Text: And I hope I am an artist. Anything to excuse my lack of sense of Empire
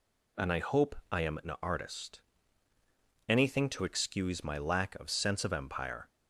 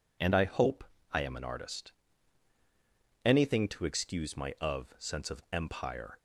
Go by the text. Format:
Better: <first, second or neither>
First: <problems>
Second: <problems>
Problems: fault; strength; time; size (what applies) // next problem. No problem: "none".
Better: first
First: pauses between "hope" and "I"; slight; at 0.9 s; 0.16 s long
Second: pauses between "hope" and "I"; slight; at 0.8 s; 0.28 s long // skips "lack"; at 4.5 s